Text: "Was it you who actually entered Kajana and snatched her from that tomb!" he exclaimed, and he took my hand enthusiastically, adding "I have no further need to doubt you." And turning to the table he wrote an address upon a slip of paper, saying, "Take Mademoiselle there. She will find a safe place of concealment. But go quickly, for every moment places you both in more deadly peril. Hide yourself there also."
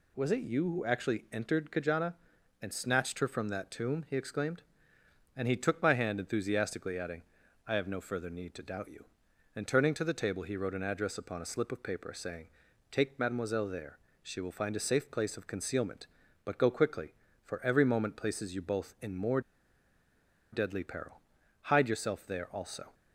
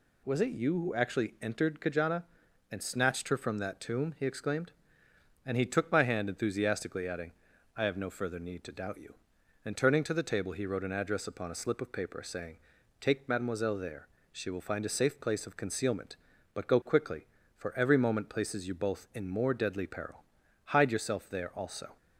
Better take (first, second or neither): second